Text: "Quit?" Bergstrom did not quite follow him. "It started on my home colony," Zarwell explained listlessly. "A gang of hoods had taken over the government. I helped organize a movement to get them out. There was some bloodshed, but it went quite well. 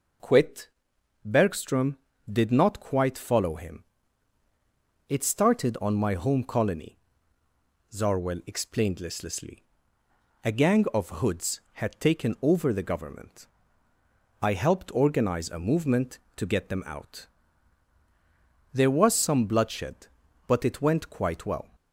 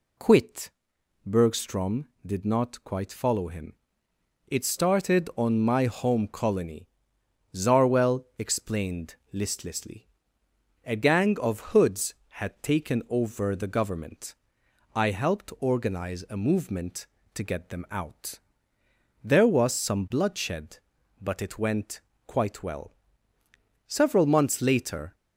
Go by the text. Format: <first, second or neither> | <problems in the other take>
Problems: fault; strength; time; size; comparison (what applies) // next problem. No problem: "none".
first | pauses between "explained" and "listlessly"; slight; at 9.1 s; 0.18 s long // pauses between "went" and "quite"; slight; at 22.0 s; 0.26 s long // goes on to say "Several months later"; noticeable; from 23.8 s on; 1.2 s long